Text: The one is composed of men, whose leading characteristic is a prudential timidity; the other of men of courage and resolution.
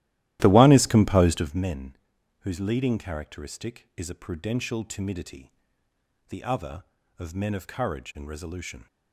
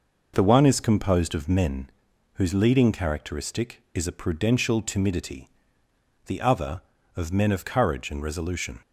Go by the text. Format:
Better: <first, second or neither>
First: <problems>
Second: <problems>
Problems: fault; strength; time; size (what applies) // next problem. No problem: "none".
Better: second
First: starts louder than the rest; strong; until 1.7 s; 15 dB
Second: none